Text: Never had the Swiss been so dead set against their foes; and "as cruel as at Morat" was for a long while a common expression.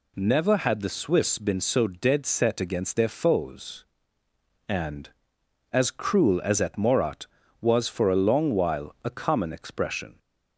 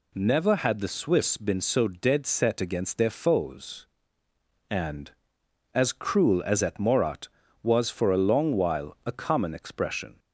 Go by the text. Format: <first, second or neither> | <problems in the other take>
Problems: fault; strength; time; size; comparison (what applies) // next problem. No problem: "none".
neither | none